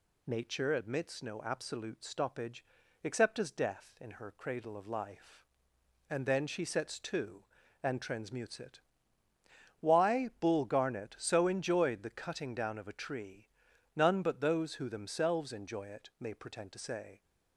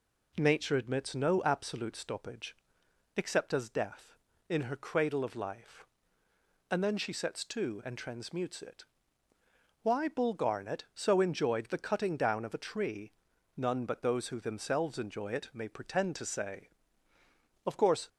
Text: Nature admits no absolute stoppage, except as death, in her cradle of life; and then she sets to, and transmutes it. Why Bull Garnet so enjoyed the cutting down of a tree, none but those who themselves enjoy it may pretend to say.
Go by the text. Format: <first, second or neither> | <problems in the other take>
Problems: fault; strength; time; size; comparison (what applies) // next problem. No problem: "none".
first | goes on to say "Of course"; slight; from 17.6 s on; 0.44 s long